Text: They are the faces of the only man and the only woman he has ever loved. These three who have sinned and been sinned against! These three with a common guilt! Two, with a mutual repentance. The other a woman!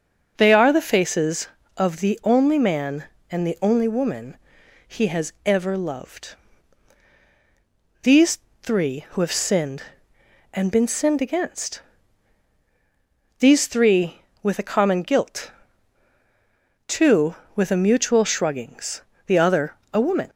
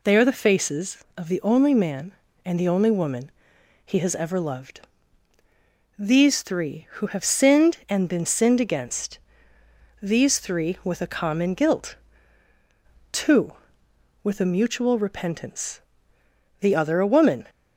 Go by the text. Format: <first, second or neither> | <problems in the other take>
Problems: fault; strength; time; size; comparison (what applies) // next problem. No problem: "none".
second | pauses between "woman" and "he"; noticeable; at 4.3 s; 0.52 s long; noticeable in the second // pauses between "These" and "three"; slight; at 8.3 s; 0.22 s long // says "shruggings" for "repentance"; at 18.2 s // pauses between "other" and "a"; slight; at 19.7 s; 0.18 s long